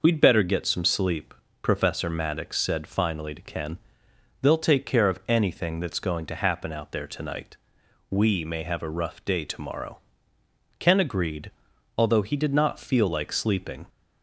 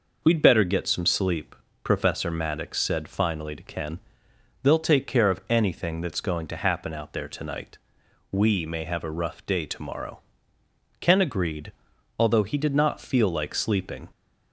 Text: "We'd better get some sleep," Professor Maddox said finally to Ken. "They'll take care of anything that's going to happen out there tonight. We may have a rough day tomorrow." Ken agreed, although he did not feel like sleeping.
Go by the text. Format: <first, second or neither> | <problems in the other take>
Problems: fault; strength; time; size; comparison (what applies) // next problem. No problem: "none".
neither | none